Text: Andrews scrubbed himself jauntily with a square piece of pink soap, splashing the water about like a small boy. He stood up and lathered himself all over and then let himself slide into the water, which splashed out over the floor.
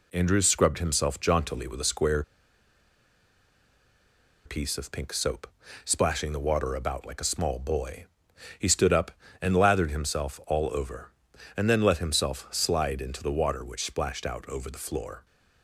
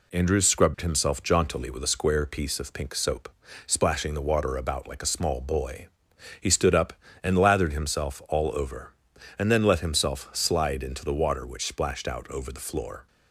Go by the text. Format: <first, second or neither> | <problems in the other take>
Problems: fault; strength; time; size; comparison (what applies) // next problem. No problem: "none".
second | pauses between "square" and "piece"; strong; at 2.2 s; 2.2 s long